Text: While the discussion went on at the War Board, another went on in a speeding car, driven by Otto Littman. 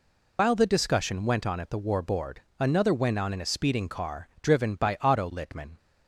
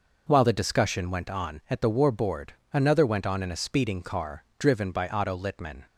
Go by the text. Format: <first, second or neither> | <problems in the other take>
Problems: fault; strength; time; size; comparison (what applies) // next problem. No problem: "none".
second | loses the start of "While"; at 0.3 s; 95 ms